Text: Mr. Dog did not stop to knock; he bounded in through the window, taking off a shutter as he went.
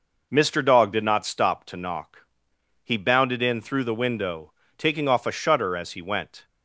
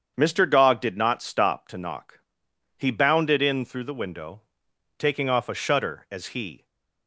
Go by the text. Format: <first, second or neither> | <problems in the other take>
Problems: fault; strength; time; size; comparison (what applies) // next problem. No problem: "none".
first | starts louder than the rest; strong; until 1.1 s; 7.5 dB // stops before "went"; at 6.6 s